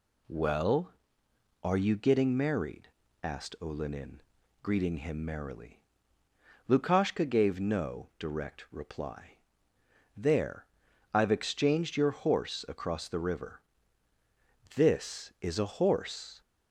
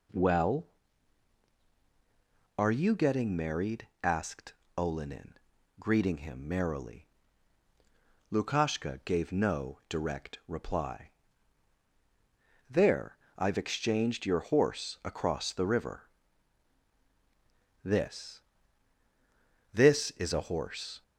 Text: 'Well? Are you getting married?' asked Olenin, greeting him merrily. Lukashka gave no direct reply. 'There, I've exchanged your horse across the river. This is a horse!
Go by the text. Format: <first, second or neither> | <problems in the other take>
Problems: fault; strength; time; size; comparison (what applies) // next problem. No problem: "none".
first | pauses between "asked" and "Olenin"; slight; at 4.5 s; 0.22 s long // says "This" twice; at 19.7 s